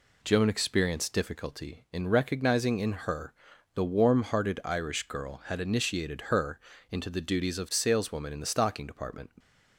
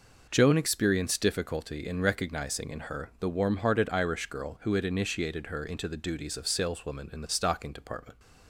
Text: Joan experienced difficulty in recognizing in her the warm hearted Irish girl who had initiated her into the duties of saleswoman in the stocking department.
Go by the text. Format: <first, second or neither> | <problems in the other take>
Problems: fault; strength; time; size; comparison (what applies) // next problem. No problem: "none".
second | pauses between "her" and "the"; at 3.3 s; 0.40 s long // skips "who"; at 5.4 s // pauses between "her" and "into"; slight; at 6.5 s; 0.32 s long